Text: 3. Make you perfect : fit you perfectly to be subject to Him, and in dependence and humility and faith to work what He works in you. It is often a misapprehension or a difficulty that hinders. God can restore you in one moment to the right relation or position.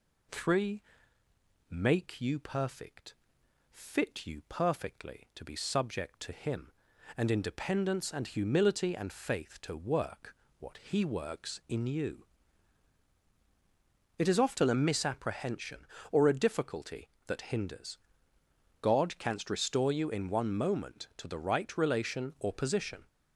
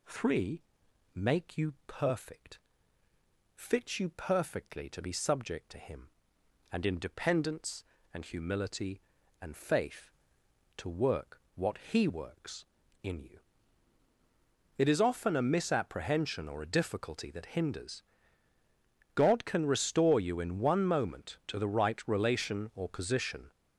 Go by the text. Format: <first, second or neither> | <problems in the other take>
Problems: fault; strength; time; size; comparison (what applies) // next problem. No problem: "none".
second | pauses between "work" and "what"; slight; at 10.3 s; 0.24 s long // says "canst" for "can"; at 19.1 s